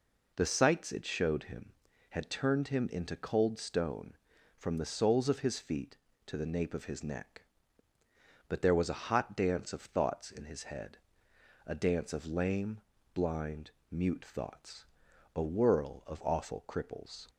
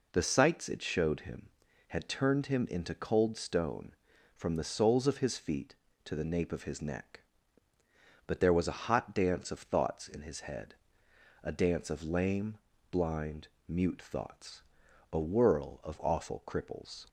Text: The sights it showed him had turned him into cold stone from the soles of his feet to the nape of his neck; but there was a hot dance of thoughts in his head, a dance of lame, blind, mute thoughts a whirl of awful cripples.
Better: neither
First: pauses between "thoughts" and "a"; noticeable; at 14.8 s; 0.50 s long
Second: pauses between "thoughts" and "a"; noticeable; at 14.6 s; 0.50 s long

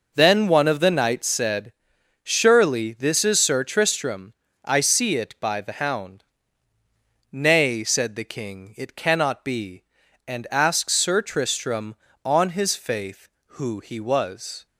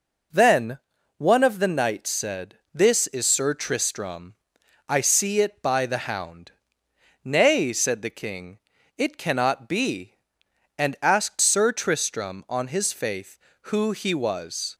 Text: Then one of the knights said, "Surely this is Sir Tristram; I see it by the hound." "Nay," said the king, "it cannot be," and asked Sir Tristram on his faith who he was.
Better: first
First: none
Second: pauses between "Then" and "one"; at 0.7 s; 0.40 s long // skips "Surely"; at 2.6 s

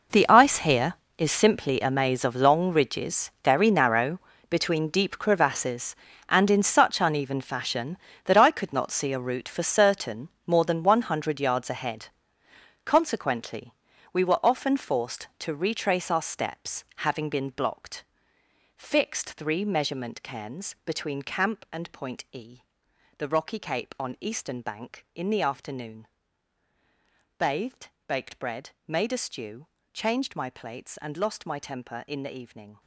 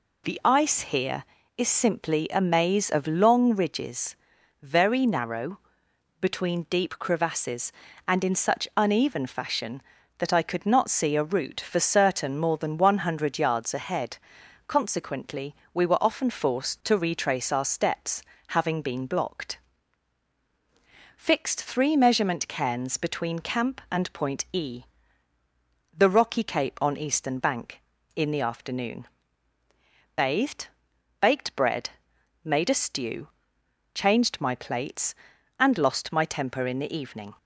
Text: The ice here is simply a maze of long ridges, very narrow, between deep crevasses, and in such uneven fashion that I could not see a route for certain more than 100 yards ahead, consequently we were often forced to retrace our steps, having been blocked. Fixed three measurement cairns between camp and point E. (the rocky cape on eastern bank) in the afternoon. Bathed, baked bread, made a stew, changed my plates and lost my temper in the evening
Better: second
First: gets quieter; strong; throughout; 16 dB // pauses between "certain" and "more"; slight; at 10.2 s; 0.18 s long // pauses between "consequently" and "we"; at 13.7 s; 0.38 s long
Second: pauses between "consequently" and "we"; slight; at 15.5 s; 0.20 s long

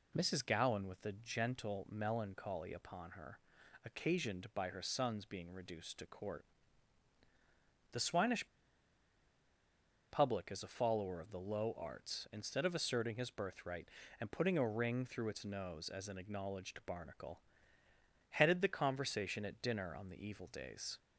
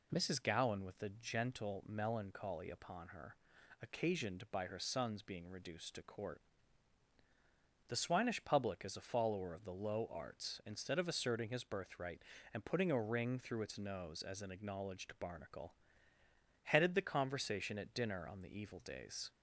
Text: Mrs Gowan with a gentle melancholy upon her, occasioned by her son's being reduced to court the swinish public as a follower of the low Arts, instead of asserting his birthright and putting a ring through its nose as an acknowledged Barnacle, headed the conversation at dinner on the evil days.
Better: second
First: pauses between "court" and "the"; strong; at 6.4 s; 1.4 s long // pauses between "swinish" and "public"; strong; at 8.4 s; 1.6 s long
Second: pauses between "court" and "the"; strong; at 6.4 s; 1.4 s long

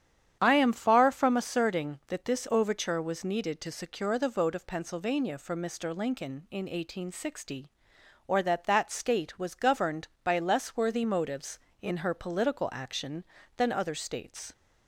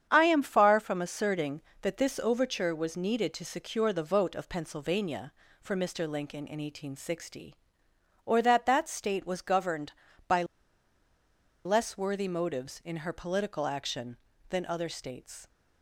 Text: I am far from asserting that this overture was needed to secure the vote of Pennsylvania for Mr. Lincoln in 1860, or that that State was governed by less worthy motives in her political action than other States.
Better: first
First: starts louder than the rest; strong; until 1.4 s; 9 dB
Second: starts louder than the rest; strong; until 1.1 s; 8.5 dB // pauses between "by" and "less"; at 10.4 s; 1.2 s long

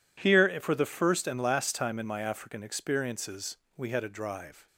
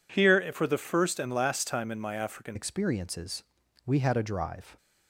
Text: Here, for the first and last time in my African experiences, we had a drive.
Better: first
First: none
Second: changes voice at "experiences"; from 2.5 s on; 2.2 s long

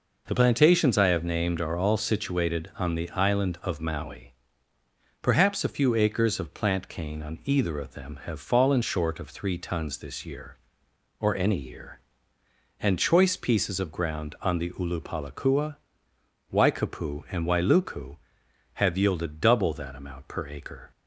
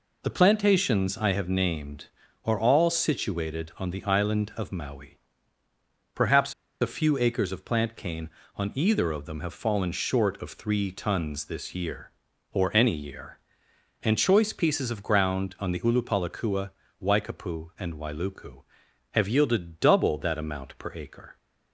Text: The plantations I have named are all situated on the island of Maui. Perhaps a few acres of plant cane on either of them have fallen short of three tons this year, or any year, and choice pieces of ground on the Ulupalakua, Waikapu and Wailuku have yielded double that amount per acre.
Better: first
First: none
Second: pauses between "Perhaps" and "a"; slight; at 6.5 s; 0.29 s long

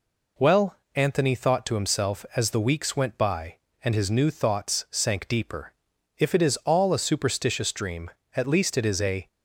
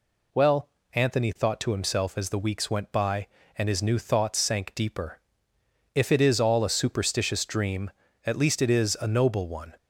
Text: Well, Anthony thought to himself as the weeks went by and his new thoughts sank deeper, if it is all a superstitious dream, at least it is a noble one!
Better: second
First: stops before "noble one"; at 9.2 s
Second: none

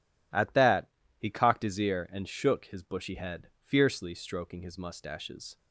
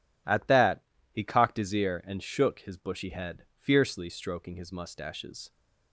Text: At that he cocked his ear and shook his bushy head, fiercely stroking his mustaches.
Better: neither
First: pauses between "that" and "he"; slight; at 0.8 s; 0.30 s long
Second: pauses between "that" and "he"; slight; at 0.8 s; 0.30 s long

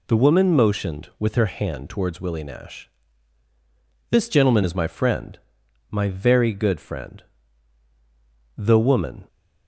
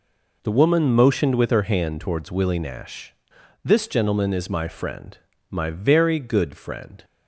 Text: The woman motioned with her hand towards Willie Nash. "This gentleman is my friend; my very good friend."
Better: second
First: goes on to say "The woman"; noticeable; from 8.5 s on; 0.70 s long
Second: none

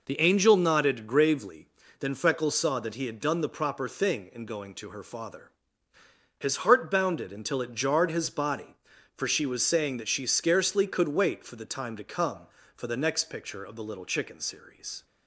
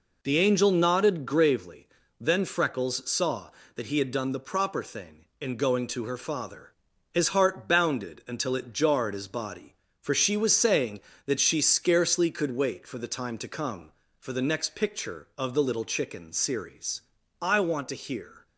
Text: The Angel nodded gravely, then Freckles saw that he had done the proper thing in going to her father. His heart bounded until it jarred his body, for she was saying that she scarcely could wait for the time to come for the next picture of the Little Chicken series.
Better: first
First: none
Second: goes on to say "I want to hear"; noticeable; from 17.4 s on; 1.0 s long

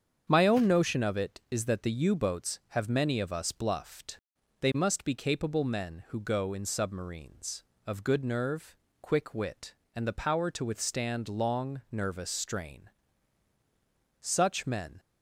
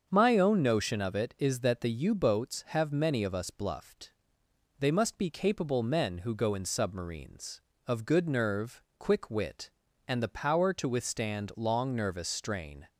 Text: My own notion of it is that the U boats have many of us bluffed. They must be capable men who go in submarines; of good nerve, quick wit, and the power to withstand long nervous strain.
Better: second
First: starts louder than the rest; strong; until 1.3 s; 7.5 dB // goes on to say "Such men"; noticeable; from 14.2 s on; 0.78 s long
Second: starts louder than the rest; until 1.1 s; 7 dB

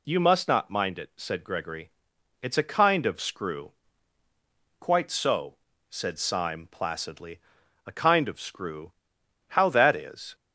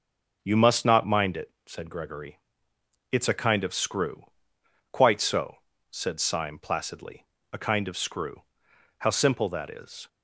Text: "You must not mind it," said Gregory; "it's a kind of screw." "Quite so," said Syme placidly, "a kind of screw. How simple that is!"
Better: second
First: skips "simple"; at 9.7 s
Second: none

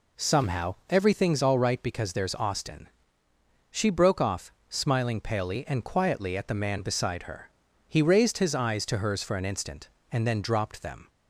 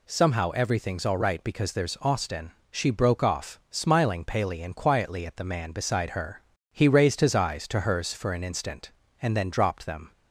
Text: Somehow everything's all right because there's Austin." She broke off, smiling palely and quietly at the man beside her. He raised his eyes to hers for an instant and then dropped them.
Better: neither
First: none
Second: none

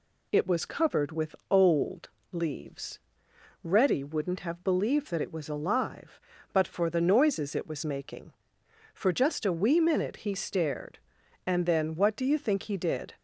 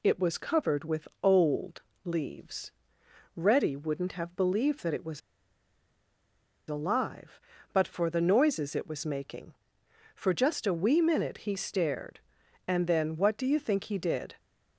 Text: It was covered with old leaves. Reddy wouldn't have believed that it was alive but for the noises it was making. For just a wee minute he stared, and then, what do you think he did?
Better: first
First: pauses between "old" and "leaves"; slight; at 2.0 s; 0.24 s long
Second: pauses between "old" and "leaves"; slight; at 1.8 s; 0.24 s long // pauses between "was" and "alive"; strong; at 5.2 s; 1.4 s long

